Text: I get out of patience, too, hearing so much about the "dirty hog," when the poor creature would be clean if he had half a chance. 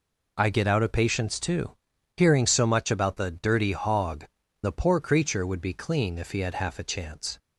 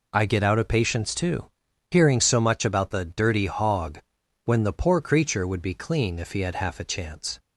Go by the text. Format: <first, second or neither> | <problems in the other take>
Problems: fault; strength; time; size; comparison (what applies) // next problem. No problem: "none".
second | skips "when"; at 4.4 s